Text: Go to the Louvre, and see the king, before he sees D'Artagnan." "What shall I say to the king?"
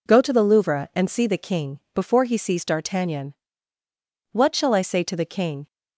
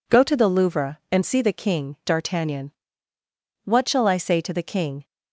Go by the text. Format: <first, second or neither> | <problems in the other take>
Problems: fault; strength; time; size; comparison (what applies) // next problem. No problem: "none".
first | skips "before he sees"; at 2.0 s